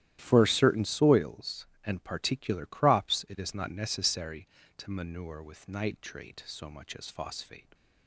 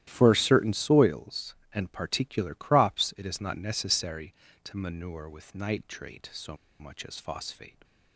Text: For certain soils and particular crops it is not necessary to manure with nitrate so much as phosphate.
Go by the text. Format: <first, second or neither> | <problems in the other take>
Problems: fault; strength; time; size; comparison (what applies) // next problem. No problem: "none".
first | starts louder than the rest; strong; until 1.0 s; 13 dB; strong in the first // pauses between "so" and "much"; slight; at 6.5 s; 0.23 s long